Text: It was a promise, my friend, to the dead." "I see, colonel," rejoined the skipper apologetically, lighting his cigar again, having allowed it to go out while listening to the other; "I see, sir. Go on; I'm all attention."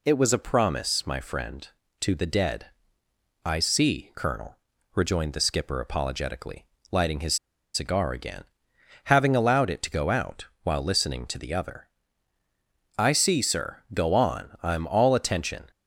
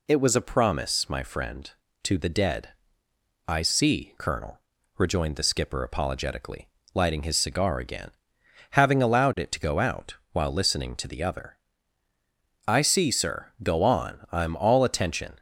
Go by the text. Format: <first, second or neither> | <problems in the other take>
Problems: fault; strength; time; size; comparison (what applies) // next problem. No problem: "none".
second | pauses between "his" and "cigar"; at 7.3 s; 0.38 s long // pauses between "out" and "while"; slight; at 10.4 s; 0.16 s long; slight in the second